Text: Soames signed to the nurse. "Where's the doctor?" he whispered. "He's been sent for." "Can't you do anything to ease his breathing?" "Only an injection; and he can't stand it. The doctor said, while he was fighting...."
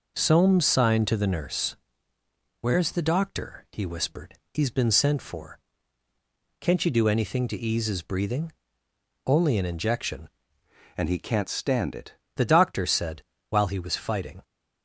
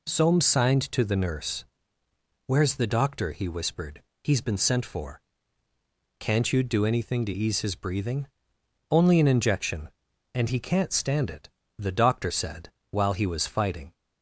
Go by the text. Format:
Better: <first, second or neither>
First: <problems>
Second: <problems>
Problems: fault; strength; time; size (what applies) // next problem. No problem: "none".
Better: second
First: changes voice from "and" to "it"; from 10.9 to 12.1 s; 1.2 s long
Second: none